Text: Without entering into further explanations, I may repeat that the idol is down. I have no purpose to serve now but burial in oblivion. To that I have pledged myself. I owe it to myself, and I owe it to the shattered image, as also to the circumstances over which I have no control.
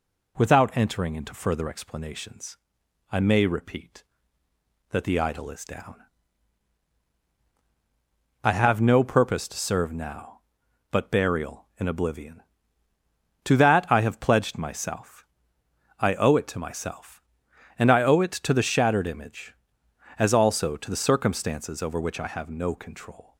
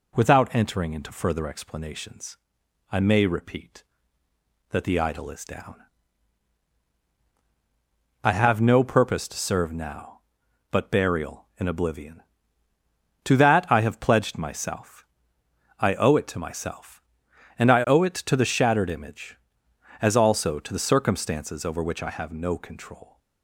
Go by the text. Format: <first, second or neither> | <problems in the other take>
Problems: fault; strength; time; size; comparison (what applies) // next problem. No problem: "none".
neither | none